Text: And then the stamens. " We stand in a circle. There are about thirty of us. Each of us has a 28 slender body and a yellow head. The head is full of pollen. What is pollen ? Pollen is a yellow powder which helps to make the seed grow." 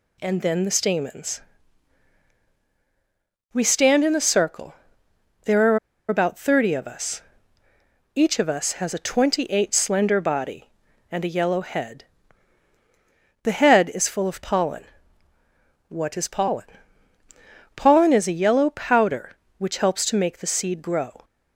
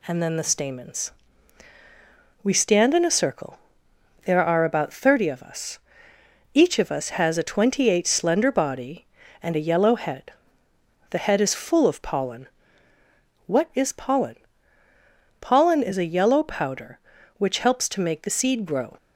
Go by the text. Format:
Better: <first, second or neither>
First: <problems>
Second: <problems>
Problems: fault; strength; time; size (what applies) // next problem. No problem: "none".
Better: second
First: pauses between "are" and "about"; slight; at 5.7 s; 0.30 s long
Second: none